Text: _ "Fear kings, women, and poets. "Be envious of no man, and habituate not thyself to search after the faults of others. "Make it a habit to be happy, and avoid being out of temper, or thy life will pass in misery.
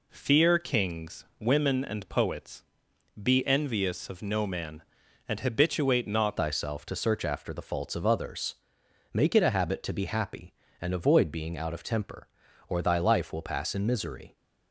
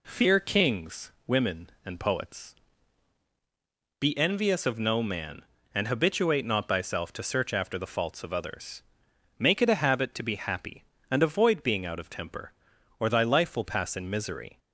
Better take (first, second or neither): second